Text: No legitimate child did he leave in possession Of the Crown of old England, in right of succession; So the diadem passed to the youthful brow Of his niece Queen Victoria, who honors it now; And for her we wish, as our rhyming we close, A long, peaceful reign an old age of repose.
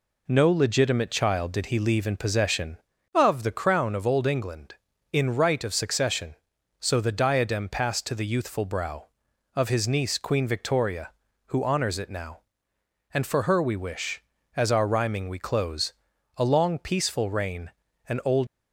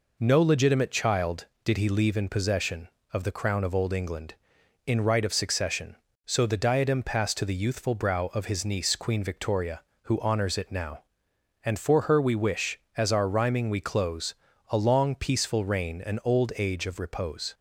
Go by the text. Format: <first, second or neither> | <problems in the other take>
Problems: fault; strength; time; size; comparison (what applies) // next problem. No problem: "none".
second | pauses between "reign" and "an"; slight; at 17.7 s; 0.36 s long // stops before "age of repose"; at 18.4 s